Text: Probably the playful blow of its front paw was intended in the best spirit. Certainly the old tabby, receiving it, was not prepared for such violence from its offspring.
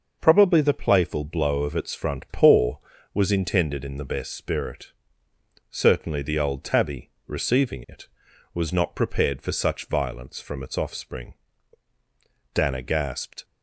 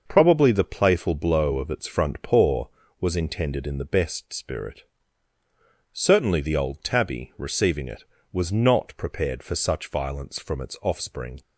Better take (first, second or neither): second